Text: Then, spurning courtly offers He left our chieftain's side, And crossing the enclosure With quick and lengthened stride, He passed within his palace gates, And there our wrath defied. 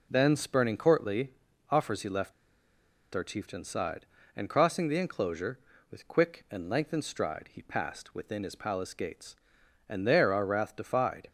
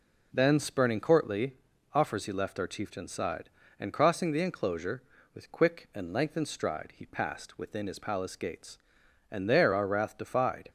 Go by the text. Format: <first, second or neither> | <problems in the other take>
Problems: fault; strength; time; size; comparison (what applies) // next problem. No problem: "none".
second | pauses between "courtly" and "offers"; at 1.3 s; 0.38 s long; also in the second // pauses between "left" and "our"; noticeable; at 2.3 s; 0.81 s long